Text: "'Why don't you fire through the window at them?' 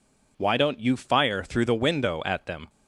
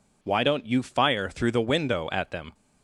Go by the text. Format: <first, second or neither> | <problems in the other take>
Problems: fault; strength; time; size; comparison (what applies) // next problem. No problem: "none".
neither | none